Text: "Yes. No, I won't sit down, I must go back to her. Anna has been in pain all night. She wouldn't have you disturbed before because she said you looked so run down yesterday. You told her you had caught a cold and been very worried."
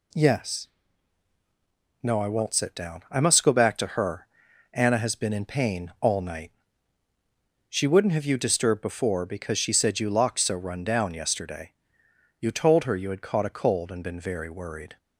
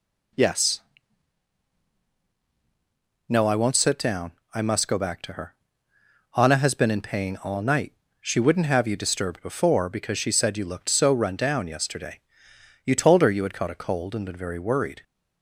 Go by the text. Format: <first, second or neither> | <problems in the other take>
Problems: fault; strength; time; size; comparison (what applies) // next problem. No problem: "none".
second | says "locked" for "looked"; at 10.0 s